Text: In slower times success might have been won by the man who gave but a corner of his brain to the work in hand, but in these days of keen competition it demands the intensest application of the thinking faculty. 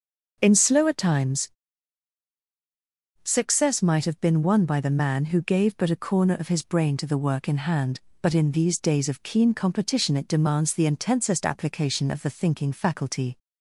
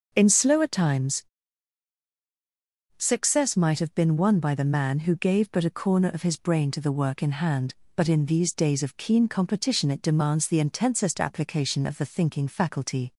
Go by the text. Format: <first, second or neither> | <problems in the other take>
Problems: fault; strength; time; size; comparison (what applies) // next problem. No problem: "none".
neither | starts louder than the rest; noticeable; the same in both // pauses between "times" and "success"; strong; the same in both